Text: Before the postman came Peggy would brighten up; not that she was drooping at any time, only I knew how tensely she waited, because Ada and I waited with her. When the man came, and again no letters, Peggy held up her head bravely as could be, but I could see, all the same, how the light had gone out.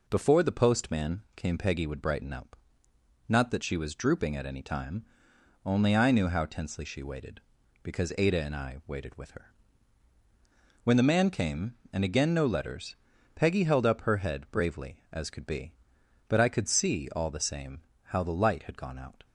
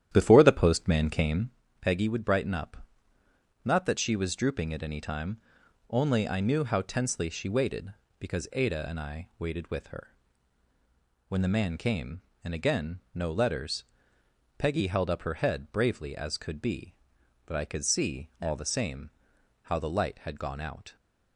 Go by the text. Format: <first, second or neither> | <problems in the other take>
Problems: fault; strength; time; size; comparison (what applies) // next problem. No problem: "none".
first | starts louder than the rest; strong; until 1.6 s; 11 dB // pauses between "came" and "Peggy"; slight; at 1.5 s; 0.30 s long